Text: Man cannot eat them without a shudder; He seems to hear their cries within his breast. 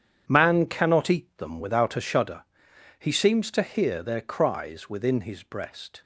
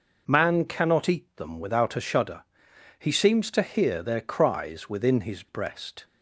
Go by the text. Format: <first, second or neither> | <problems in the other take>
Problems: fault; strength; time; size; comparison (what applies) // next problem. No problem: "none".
second | gets quieter; strong; throughout; 10.5 dB